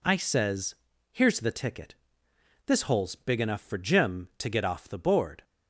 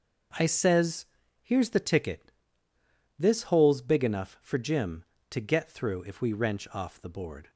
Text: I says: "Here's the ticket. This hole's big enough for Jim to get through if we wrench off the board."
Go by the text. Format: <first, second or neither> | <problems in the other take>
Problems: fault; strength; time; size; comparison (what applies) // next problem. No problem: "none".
second | skips "through if we wrench"; at 4.6 s